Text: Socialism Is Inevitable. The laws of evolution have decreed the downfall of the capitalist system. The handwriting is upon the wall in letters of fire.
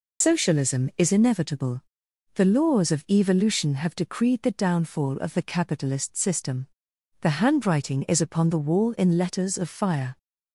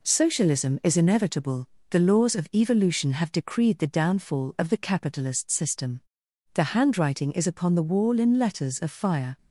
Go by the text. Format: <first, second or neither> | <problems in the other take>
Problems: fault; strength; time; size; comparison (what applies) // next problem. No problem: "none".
second | loses the start of "Socialism"; at 0.2 s; 120 ms